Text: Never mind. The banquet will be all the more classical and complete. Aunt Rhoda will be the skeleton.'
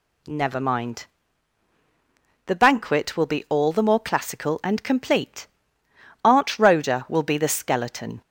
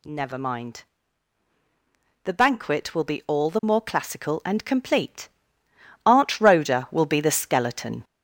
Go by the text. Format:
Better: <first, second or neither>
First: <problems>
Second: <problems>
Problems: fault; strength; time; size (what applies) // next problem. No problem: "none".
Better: first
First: none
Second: gets louder; noticeable; throughout; 6 dB